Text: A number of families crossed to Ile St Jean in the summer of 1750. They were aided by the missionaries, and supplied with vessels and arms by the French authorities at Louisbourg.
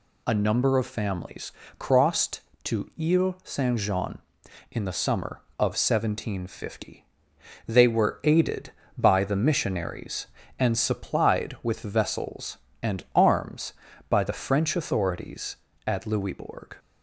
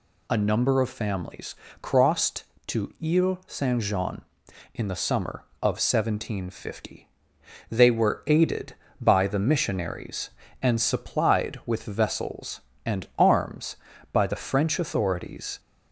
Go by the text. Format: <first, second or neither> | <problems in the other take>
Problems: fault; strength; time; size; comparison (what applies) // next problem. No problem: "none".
first | pauses between "families" and "crossed"; slight; at 1.5 s; 0.24 s long; slight in the first // stops before "at Louisbourg"; at 15.5 s